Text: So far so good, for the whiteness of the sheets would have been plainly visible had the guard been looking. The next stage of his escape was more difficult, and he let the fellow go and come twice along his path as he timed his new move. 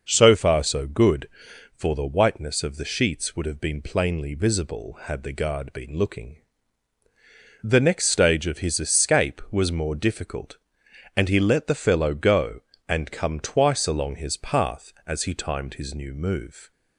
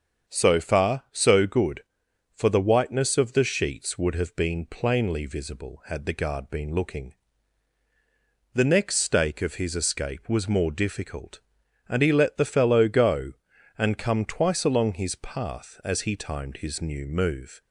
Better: first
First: none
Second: starts louder than the rest; strong; until 1.3 s; 7 dB // says "stake" for "stage"; at 8.9 s

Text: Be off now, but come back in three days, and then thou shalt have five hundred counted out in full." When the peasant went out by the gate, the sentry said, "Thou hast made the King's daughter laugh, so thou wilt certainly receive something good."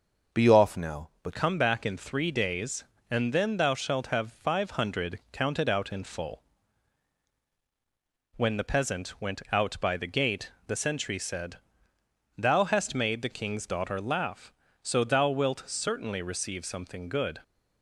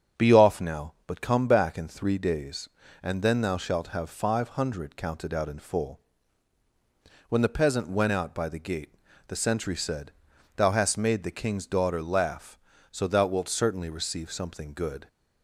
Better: second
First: starts louder than the rest; noticeable; until 1.4 s; 6 dB // changes voice at "come"; from 1.3 s on; 16.1 s long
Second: starts louder than the rest; strong; until 1.3 s; 7.5 dB

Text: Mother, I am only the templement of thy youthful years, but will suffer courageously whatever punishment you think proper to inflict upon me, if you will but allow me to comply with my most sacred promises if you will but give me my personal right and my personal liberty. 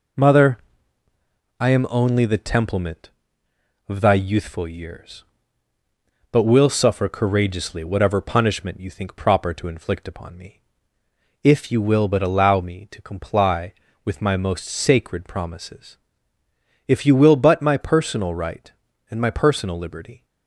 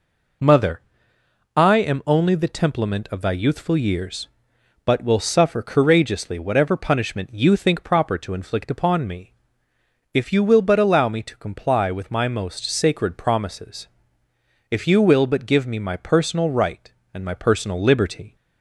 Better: second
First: pauses between "promises" and "if"; noticeable; at 15.9 s; 0.90 s long // skips "give me"; at 17.6 s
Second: pauses between "promises" and "if"; noticeable; at 13.8 s; 0.84 s long

